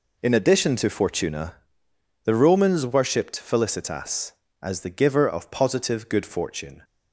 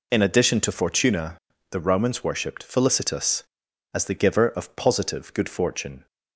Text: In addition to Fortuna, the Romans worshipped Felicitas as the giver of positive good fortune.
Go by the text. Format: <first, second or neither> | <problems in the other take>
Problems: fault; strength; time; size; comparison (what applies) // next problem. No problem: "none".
neither | none